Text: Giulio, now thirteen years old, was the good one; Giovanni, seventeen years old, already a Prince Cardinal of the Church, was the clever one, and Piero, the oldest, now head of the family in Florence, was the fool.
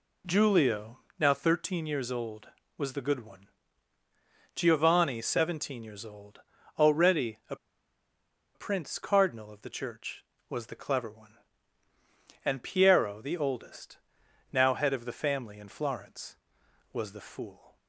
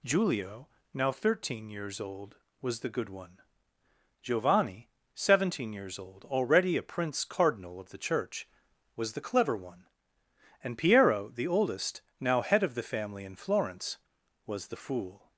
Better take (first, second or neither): second